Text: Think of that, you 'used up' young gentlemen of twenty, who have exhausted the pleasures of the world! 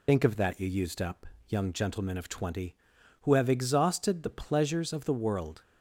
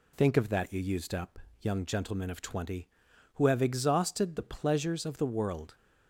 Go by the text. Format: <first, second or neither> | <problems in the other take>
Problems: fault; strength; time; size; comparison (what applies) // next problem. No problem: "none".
second | loses the start of "Think"; at 0.0 s; 80 ms // pauses between "up" and "young"; slight; at 1.2 s; 0.20 s long; slight in the second